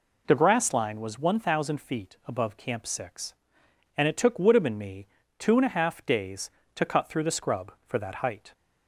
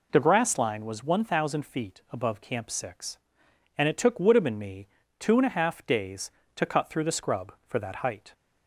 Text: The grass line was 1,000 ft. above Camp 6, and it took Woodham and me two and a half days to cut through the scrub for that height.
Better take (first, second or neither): neither